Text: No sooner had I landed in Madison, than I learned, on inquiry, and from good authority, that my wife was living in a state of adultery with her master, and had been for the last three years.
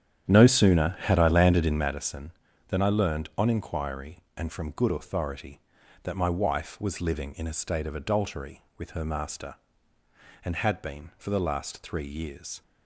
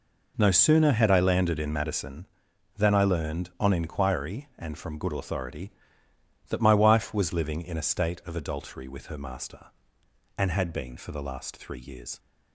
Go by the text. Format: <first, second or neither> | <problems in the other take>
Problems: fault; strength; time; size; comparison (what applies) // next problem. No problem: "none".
second | starts louder than the rest; strong; until 1.9 s; 9.5 dB